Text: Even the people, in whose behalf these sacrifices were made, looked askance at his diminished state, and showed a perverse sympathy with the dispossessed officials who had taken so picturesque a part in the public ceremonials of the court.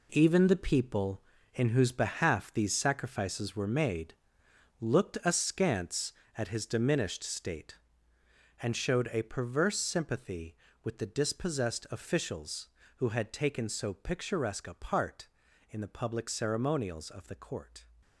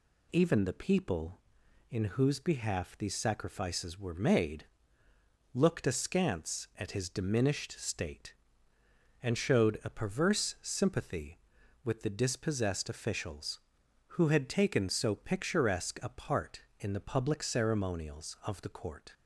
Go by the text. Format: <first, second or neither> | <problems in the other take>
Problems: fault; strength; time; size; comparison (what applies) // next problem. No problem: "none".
second | gets quieter; strong; throughout; 10 dB